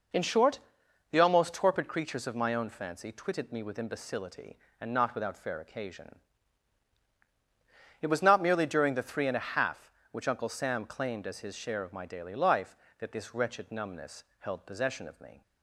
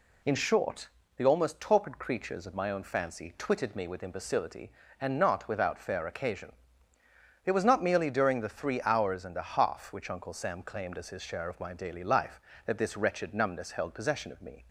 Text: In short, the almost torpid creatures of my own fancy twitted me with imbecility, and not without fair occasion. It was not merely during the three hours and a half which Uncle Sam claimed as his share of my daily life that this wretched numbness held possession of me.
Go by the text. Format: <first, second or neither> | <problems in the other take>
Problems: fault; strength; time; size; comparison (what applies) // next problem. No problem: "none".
second | skips "hours"; at 9.2 s // pauses between "numbness" and "held"; slight; at 14.2 s; 0.16 s long